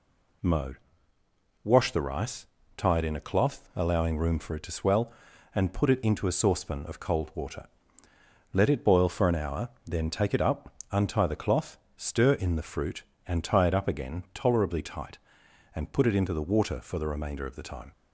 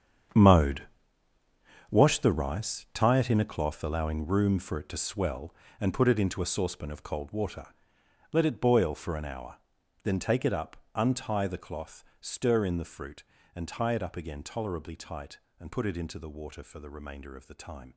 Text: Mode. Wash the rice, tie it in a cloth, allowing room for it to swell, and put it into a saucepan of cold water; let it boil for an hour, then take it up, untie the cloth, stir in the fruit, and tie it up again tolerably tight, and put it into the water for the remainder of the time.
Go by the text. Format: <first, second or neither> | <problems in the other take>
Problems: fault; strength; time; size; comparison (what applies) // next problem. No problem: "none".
first | gets quieter; strong; throughout; 14 dB